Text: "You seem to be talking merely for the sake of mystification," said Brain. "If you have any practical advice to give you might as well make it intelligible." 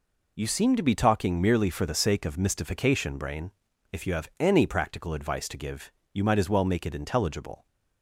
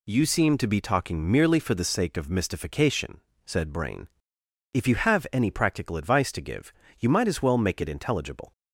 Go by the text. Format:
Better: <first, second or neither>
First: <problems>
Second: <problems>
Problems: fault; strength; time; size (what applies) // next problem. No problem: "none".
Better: second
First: skips "said"; at 3.1 s // pauses between "give" and "you"; slight; at 5.9 s; 0.20 s long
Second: pauses between "give" and "you"; slight; at 6.7 s; 0.26 s long